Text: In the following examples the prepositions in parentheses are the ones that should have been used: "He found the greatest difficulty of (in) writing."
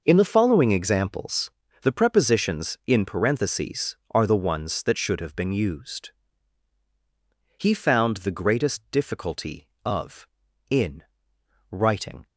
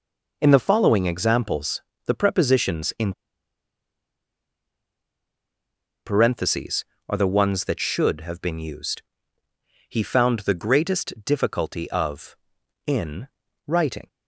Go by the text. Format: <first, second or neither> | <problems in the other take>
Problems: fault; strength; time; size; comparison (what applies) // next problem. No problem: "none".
first | pauses between "examples" and "the"; slight; at 1.8 s; 0.26 s long; slight in the first // pauses between "in" and "parentheses"; strong; at 3.1 s; 2.9 s long